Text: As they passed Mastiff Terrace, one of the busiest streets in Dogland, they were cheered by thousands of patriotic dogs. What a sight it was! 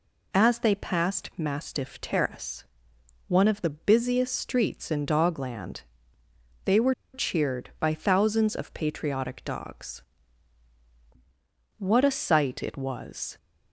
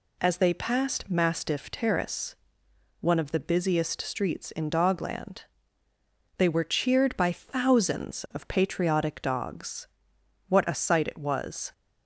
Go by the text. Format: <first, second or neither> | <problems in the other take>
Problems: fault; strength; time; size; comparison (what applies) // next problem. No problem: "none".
second | pauses between "were" and "cheered"; slight; at 6.9 s; 0.20 s long